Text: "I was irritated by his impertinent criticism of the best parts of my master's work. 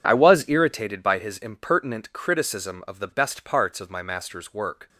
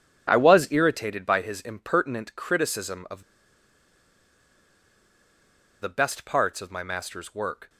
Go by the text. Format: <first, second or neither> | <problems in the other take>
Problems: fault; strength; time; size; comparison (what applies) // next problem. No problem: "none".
first | pauses between "of" and "the"; strong; at 3.2 s; 2.5 s long